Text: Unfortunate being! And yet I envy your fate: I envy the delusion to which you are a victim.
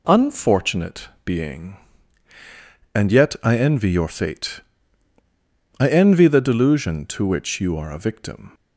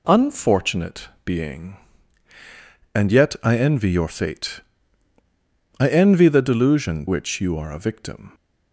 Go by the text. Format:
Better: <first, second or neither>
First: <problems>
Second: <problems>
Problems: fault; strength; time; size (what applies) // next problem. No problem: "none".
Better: first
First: pauses between "Unfortunate" and "being"; slight; at 1.0 s; 0.16 s long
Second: pauses between "Unfortunate" and "being"; slight; at 1.0 s; 0.16 s long // skips "to"; at 7.0 s